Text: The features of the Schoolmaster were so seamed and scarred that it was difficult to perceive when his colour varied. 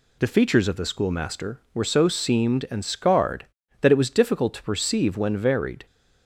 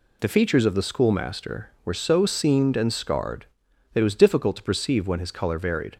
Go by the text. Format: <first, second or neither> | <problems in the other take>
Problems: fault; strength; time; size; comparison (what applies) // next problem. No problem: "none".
second | skips "his colour"; at 5.3 s